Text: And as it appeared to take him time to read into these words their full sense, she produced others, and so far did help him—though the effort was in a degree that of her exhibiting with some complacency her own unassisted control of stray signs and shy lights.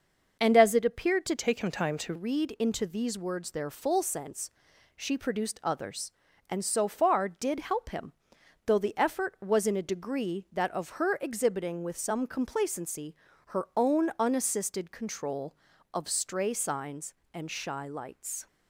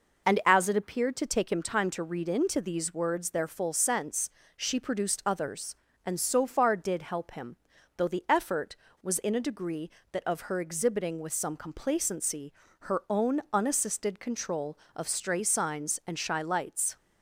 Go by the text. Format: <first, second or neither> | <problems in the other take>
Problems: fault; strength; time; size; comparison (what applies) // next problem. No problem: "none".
second | starts louder than the rest; noticeable; until 1.4 s; 6 dB // changes voice from "take" to "to"; from 1.3 to 2.1 s; 0.8 s long // pauses between "complacency" and "her"; slight; at 13.1 s; 0.34 s long; slight in the second